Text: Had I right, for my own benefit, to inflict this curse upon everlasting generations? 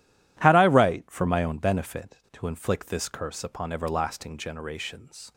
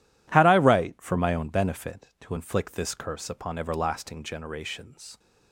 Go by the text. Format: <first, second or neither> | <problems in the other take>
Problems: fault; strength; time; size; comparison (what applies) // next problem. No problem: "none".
neither | none